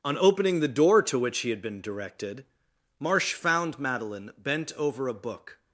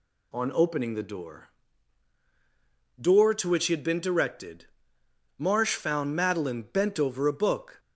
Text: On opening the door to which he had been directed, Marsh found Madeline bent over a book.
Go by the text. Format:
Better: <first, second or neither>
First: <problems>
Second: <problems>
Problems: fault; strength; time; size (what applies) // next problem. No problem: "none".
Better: first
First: none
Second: says "door" twice; at 2.9 s